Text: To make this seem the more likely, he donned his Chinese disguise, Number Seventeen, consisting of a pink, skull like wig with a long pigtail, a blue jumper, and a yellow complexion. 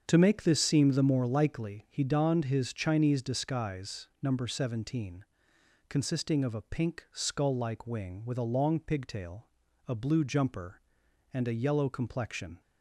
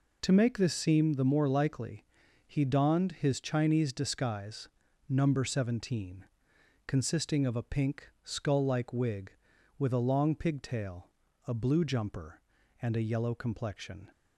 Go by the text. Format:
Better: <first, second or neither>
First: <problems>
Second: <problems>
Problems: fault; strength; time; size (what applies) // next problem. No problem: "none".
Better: second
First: starts louder than the rest; strong; until 1.0 s; 7.5 dB // says "wing" for "wig"; at 7.8 s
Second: none